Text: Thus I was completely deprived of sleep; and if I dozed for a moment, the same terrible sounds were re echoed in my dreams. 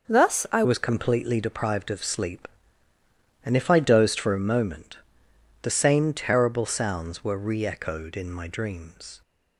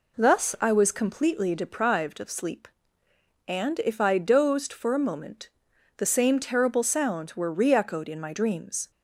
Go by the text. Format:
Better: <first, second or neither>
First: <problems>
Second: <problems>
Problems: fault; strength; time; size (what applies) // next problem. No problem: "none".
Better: second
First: changes voice at "was"; from 0.6 s on; 8.6 s long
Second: none